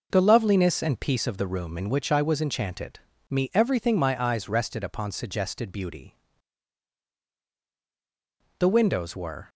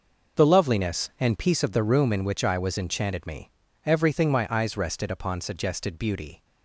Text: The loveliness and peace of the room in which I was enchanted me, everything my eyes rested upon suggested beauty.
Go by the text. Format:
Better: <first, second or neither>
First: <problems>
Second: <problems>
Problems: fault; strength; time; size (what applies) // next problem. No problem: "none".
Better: second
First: pauses between "enchanted" and "me"; slight; at 2.9 s; 0.34 s long // goes on to say "The windows were"; noticeable; from 8.5 s on; 0.92 s long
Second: none